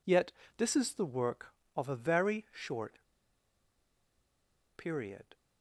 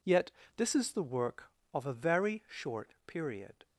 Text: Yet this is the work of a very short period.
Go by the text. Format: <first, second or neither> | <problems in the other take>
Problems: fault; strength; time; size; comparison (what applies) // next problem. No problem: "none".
second | pauses between "Yet" and "this"; slight; at 0.3 s; 0.26 s long; slight in the second // pauses between "short" and "period"; strong; at 2.9 s; 1.7 s long